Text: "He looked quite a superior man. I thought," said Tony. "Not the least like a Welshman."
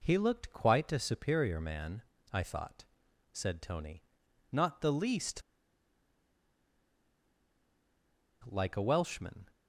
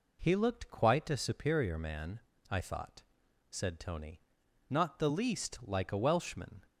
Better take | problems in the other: second | pauses between "least" and "like"; strong; at 5.4 s; 3.0 s long

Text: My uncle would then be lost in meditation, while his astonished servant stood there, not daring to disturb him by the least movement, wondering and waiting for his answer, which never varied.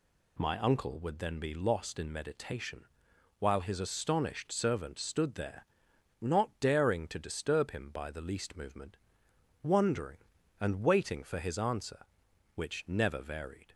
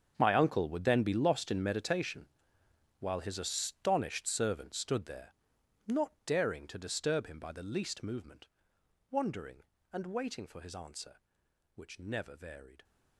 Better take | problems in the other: first | gets quieter; strong; throughout; 16 dB

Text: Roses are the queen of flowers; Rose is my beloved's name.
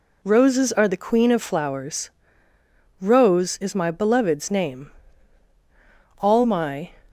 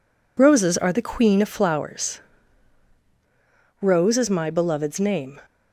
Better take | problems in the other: second | goes on to say "All my"; noticeable; from 6.1 s on; 0.70 s long

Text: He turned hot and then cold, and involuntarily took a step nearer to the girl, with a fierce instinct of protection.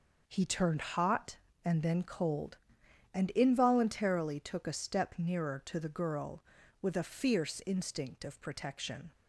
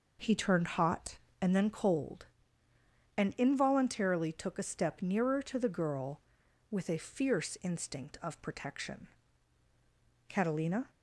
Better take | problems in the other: first | goes on to say "Catalina"; noticeable; from 10.2 s on; 0.62 s long

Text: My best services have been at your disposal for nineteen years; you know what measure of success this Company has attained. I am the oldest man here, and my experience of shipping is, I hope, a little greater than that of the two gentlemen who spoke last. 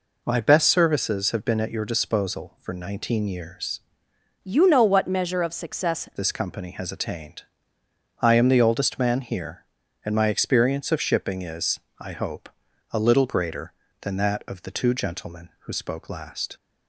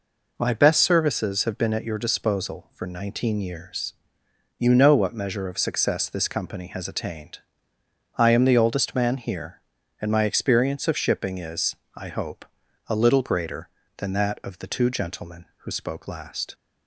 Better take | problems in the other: second | changes voice from "you" to "success"; from 4.4 to 6.1 s; 1.7 s long

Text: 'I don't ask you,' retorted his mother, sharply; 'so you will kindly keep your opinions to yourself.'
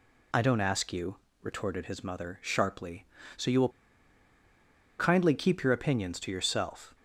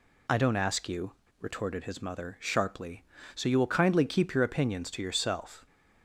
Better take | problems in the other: second | pauses between "will" and "kindly"; strong; at 3.6 s; 1.2 s long

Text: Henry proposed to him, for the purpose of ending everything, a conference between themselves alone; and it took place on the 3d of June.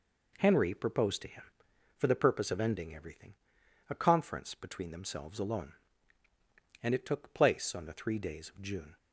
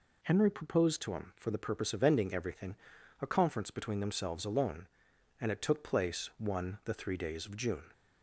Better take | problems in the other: first | says "one" for "on"; at 6.3 s

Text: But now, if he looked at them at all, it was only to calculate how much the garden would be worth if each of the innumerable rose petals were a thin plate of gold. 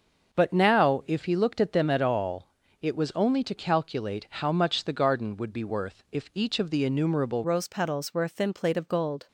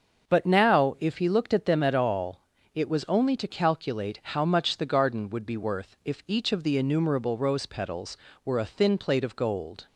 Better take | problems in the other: second | starts louder than the rest; noticeable; until 1.4 s; 6 dB; also in the second // changes voice at "rose"; from 7.4 s on; 1.8 s long

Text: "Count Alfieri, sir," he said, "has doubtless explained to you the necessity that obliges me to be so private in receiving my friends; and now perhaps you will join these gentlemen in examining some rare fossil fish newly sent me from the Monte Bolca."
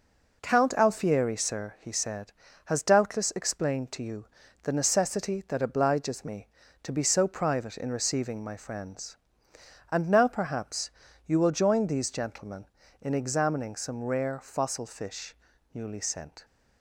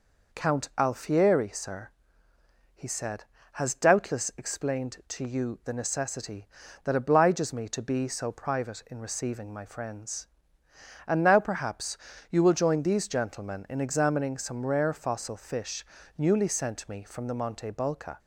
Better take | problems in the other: second | pauses between "you" and "the"; at 4.2 s; 0.38 s long // pauses between "perhaps" and "you"; slight; at 10.9 s; 0.34 s long; slight in the second // pauses between "fish" and "newly"; at 15.3 s; 0.38 s long; slight in the second // stops before "me from the Monte Bolca"; at 16.4 s

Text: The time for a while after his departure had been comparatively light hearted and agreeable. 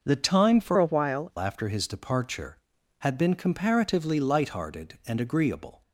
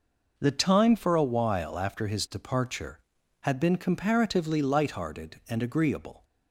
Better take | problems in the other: second | changes voice from "a" to "while"; from 0.7 to 1.3 s; 0.6 s long

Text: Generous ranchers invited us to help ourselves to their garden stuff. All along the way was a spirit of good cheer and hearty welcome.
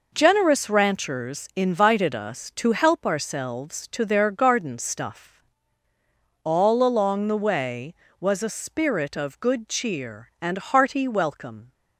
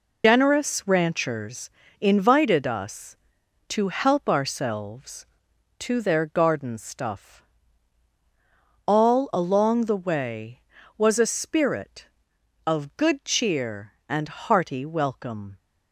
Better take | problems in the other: first | loses the start of "Generous"; at 0.2 s; 120 ms // pauses between "ranchers" and "invited"; slight; at 1.7 s; 0.30 s long

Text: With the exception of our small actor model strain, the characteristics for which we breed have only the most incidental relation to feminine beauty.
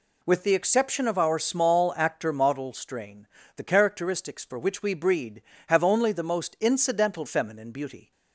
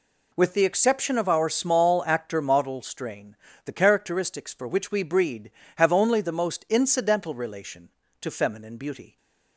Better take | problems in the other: second | skips "relation to"; at 7.2 s

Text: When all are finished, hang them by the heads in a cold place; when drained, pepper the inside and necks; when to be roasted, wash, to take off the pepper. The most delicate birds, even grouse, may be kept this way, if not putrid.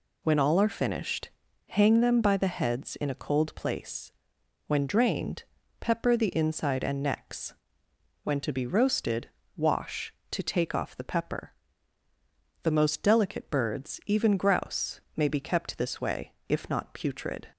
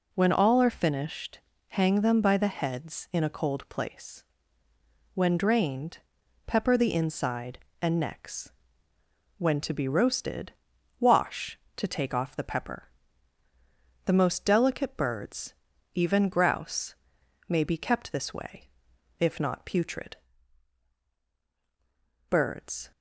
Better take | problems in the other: first | goes on to say "Birds"; noticeable; from 22.2 s on; 0.62 s long

